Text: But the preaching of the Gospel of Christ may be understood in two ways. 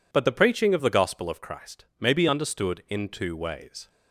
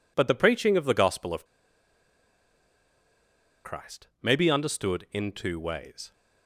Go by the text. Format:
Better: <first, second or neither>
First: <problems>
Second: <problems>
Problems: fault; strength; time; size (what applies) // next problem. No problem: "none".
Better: first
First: pauses between "Christ" and "may"; slight; at 1.8 s; 0.16 s long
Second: pauses between "of" and "Christ"; strong; at 1.4 s; 2.2 s long // pauses between "Christ" and "may"; slight; at 4.0 s; 0.16 s long